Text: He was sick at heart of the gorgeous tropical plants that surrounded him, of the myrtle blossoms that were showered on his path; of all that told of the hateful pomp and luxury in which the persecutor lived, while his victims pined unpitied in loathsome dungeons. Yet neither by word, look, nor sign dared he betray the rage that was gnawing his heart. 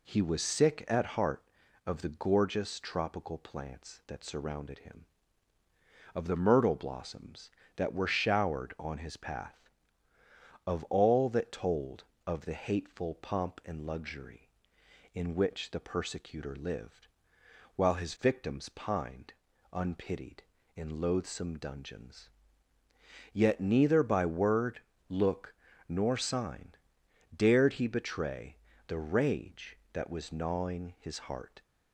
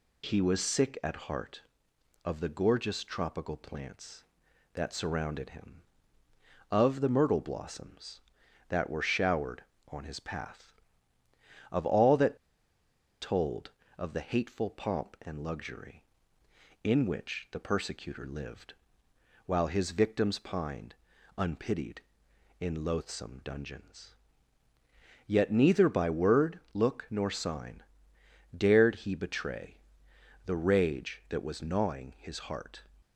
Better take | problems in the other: first | pauses between "that" and "told"; noticeable; at 12.3 s; 0.84 s long // pauses between "pined" and "unpitied"; noticeable; at 20.9 s; 0.46 s long; also in the first // pauses between "sign" and "dared"; noticeable; at 27.8 s; 0.72 s long; noticeable in the first // pauses between "betray" and "the"; noticeable; at 29.7 s; 0.70 s long; slight in the first

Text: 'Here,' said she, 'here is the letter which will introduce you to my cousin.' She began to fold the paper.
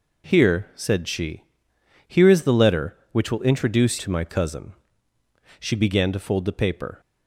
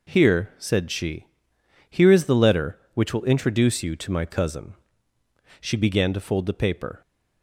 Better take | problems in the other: second | skips "you"; at 3.9 s

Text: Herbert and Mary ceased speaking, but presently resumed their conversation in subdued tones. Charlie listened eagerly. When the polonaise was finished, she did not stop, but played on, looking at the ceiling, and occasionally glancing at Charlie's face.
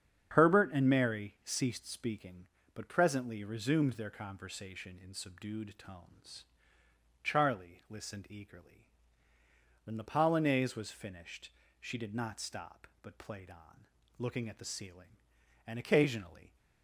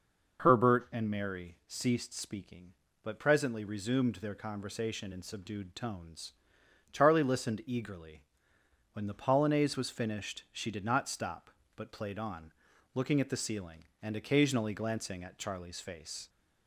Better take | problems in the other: second | starts louder than the rest; strong; until 1.4 s; 8 dB // stops before "glancing at Charlie's face"; at 16.5 s

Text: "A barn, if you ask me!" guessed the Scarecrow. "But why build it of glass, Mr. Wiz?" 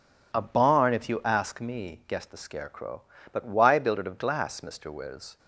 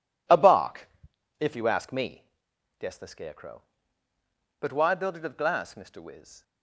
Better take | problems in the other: first | says "bark" for "barn"; at 0.3 s

